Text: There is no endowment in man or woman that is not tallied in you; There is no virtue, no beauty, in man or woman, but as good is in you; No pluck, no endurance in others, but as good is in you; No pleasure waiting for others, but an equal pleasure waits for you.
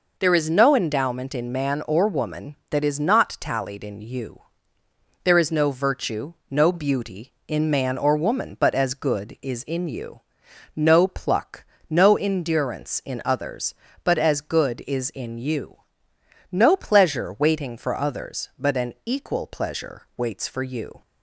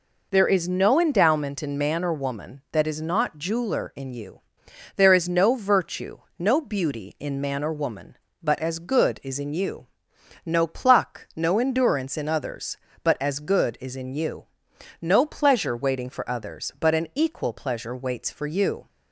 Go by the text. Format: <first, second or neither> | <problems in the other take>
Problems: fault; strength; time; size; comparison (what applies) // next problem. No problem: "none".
first | says "jeweler" for "tallied"; at 3.3 s